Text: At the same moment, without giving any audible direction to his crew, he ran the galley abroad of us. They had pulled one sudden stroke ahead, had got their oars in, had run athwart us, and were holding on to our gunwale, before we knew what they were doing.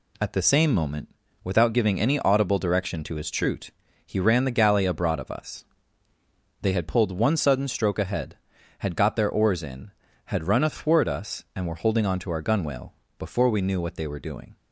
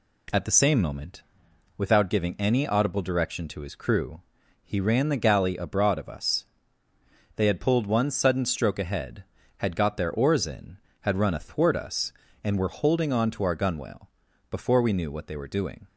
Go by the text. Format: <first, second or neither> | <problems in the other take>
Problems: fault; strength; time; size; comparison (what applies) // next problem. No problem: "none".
second | says "troot" for "crew"; at 3.2 s